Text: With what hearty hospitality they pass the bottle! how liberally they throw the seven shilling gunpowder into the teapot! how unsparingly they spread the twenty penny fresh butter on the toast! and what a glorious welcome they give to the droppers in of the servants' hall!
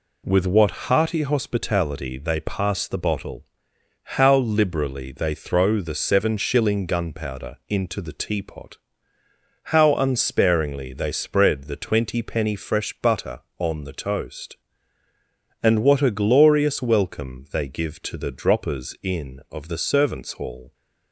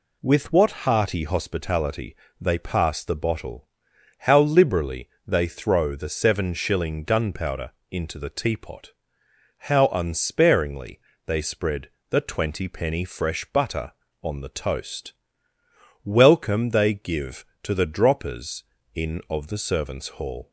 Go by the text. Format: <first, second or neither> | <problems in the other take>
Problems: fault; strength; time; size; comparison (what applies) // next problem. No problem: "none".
first | pauses between "hospitality" and "they"; slight; at 2.1 s; 0.24 s long // pauses between "liberally" and "they"; slight; at 5.0 s; 0.20 s long // pauses between "gunpowder" and "into"; slight; at 7.6 s; 0.22 s long // pauses between "unsparingly" and "they"; slight; at 10.9 s; 0.30 s long // pauses between "spread" and "the"; slight; at 11.8 s; 0.20 s long // skips "and what a glorious"; at 15.5 s